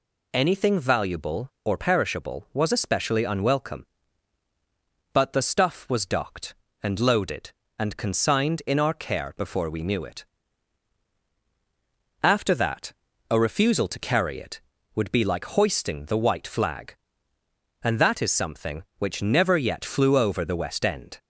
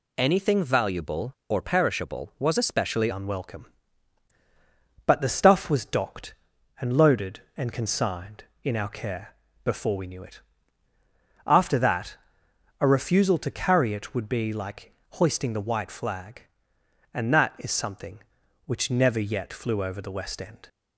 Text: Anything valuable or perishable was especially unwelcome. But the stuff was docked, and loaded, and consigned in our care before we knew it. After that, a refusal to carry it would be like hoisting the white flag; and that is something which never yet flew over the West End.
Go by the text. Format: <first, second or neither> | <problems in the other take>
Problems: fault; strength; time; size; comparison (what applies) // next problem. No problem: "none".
first | changes voice at "unwelcome"; from 3.1 s on; 17.5 s long // pauses between "care" and "before"; slight; at 9.3 s; 0.30 s long // pauses between "like" and "hoisting"; slight; at 14.9 s; 0.20 s long